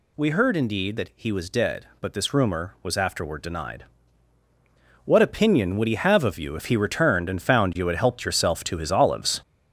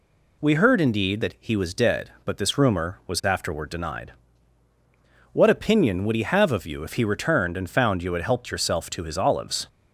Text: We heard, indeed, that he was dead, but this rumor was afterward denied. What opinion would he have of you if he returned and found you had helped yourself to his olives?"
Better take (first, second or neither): second